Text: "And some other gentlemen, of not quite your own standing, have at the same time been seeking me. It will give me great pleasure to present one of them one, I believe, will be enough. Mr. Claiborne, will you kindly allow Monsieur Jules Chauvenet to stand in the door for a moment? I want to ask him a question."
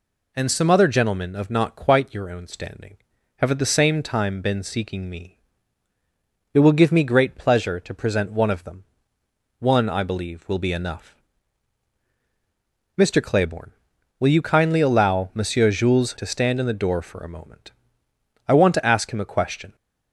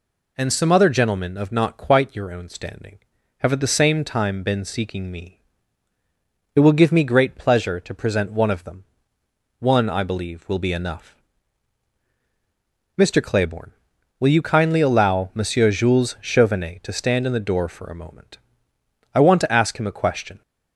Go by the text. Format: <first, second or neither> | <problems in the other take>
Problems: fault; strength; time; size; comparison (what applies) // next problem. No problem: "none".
second | pauses between "them" and "one"; noticeable; at 8.8 s; 0.76 s long; noticeable in the second // skips "Chauvenet"; at 16.1 s